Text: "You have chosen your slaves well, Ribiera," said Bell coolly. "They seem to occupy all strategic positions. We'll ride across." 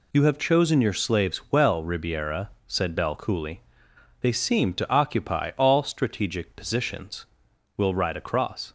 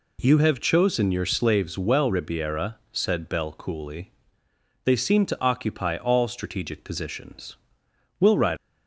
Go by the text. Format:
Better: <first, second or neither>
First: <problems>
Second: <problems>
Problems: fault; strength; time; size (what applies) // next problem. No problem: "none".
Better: first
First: none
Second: stops before "across"; at 8.5 s